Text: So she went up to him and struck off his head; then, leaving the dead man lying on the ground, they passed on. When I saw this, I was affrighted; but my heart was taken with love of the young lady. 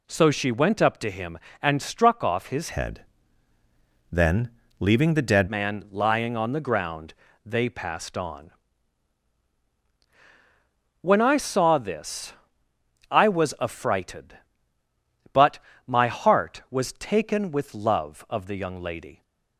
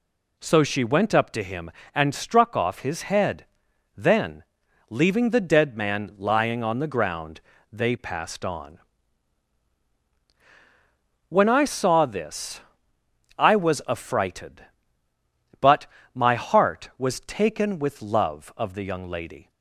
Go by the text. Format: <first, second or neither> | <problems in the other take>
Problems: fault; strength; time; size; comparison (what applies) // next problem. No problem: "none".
second | changes voice from "head" to "dead"; from 2.7 to 5.4 s; 2.7 s long // pauses between "but" and "my"; slight; at 15.6 s; 0.26 s long; slight in the second